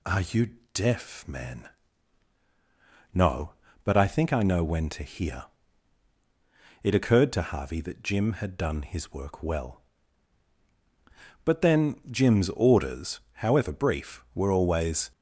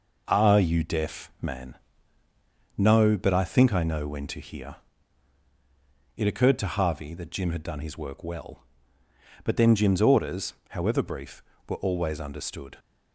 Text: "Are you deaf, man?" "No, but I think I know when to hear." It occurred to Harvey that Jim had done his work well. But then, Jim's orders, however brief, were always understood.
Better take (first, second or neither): second